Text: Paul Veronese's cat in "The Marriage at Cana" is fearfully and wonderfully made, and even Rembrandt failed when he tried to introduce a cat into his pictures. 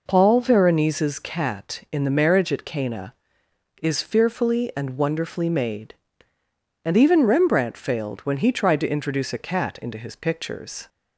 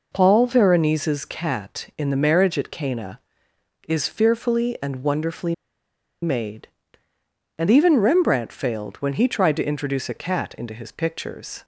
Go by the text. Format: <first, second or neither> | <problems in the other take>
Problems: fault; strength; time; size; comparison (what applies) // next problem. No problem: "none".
first | pauses between "wonderfully" and "made"; noticeable; at 5.5 s; 0.67 s long